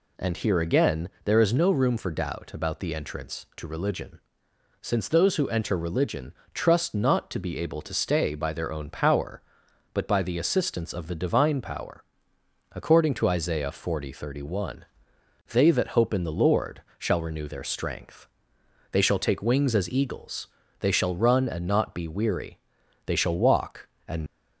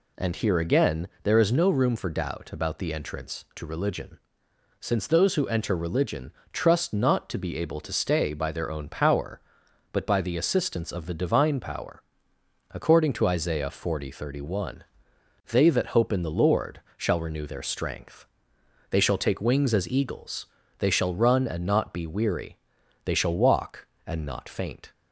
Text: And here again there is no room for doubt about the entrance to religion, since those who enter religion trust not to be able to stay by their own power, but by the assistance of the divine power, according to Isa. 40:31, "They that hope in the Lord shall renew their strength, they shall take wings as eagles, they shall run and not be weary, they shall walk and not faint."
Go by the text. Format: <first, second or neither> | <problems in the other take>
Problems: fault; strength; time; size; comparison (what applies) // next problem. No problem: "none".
second | pauses between "again" and "there"; slight; at 1.0 s; 0.16 s long; slight in the second // pauses between "religion" and "trust"; slight; at 6.3 s; 0.22 s long; slight in the second // pauses between "Lord" and "shall"; slight; at 16.7 s; 0.18 s long; slight in the second // stops before "not faint"; at 24.2 s